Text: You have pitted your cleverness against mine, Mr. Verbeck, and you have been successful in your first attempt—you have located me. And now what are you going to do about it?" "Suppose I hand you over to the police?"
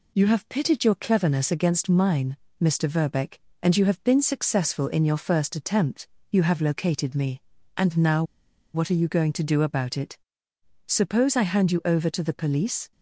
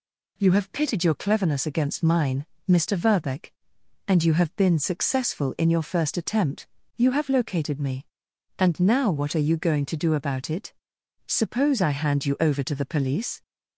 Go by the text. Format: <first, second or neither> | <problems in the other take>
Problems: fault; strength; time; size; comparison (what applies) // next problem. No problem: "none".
second | pauses between "now" and "what"; noticeable; at 8.2 s; 0.51 s long